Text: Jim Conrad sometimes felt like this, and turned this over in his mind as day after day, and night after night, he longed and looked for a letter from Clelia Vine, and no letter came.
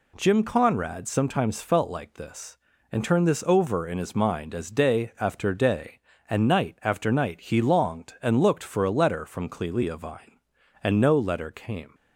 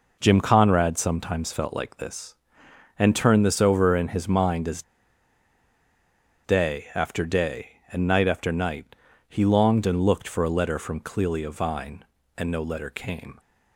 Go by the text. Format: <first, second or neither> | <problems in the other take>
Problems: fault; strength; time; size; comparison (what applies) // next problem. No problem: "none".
first | pauses between "as" and "day"; strong; at 4.8 s; 1.6 s long